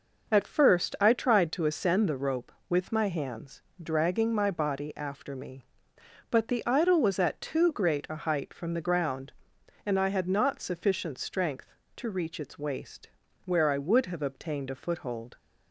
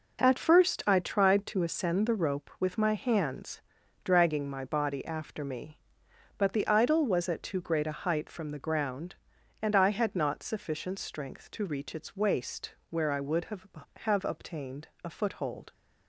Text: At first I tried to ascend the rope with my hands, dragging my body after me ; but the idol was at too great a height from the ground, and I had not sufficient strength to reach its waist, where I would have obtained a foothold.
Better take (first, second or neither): first